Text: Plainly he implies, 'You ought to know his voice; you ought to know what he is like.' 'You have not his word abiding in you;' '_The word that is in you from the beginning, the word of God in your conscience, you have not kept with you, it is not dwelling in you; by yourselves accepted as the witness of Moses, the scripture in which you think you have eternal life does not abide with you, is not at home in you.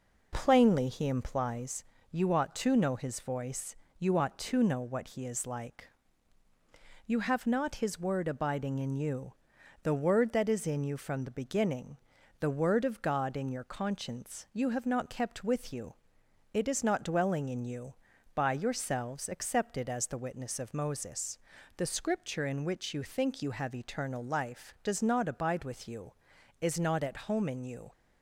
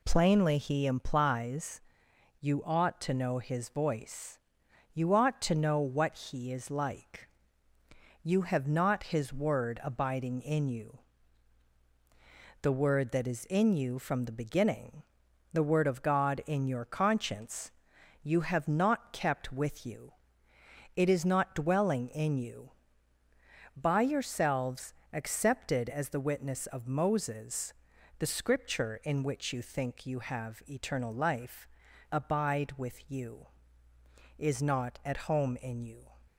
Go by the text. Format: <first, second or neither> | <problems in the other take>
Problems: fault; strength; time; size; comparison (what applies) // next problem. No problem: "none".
first | pauses between "yourselves" and "accepted"; slight; at 24.9 s; 0.20 s long // skips "does not"; at 31.8 s